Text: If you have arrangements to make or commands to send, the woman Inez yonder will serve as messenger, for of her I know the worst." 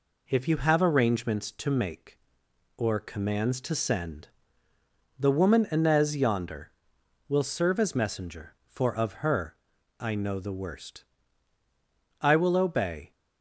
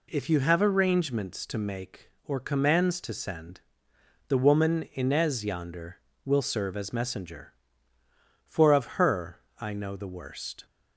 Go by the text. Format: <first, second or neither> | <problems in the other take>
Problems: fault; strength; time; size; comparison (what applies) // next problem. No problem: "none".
second | pauses between "her" and "I"; noticeable; at 9.5 s; 0.46 s long; slight in the second // goes on to say "I will obey"; noticeable; from 12.2 s on; 0.92 s long